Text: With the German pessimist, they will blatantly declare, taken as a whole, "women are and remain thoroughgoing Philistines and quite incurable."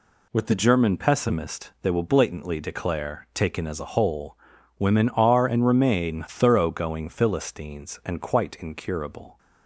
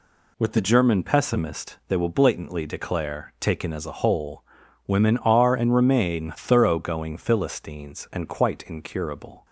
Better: neither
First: none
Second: none

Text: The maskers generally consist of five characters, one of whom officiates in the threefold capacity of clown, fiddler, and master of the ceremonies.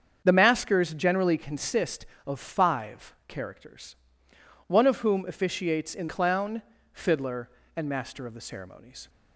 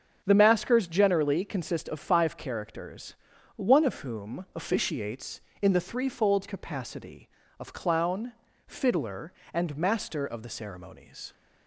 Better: second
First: starts louder than the rest; strong; until 1.2 s; 7 dB // skips "the threefold capacity of"; at 6.0 s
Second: starts louder than the rest; until 1.2 s; 7 dB

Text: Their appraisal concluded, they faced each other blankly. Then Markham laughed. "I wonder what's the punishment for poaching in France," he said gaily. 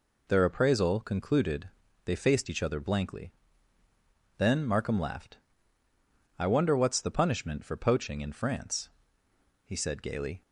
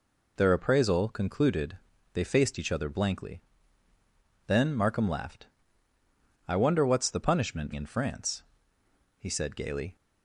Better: first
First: none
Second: skips "for poaching"; at 7.7 s

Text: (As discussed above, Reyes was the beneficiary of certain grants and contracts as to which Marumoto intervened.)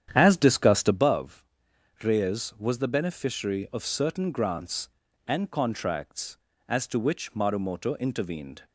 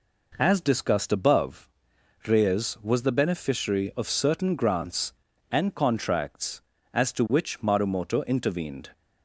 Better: second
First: starts louder than the rest; strong; until 1.1 s; 9.5 dB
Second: none

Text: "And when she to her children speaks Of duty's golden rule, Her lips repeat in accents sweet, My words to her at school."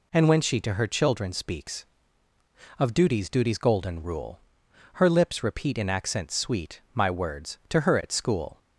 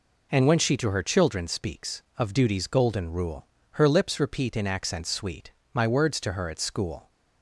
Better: second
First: says "duty's" twice; at 3.2 s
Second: none

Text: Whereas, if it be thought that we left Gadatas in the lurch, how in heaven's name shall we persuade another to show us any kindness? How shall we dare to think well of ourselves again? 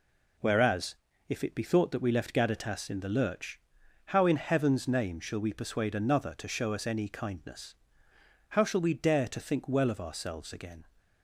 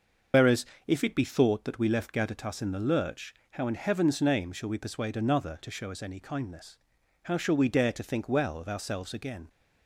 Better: first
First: none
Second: loses the start of "Whereas"; at 0.3 s; 70 ms // starts louder than the rest; until 1.5 s; 6.5 dB

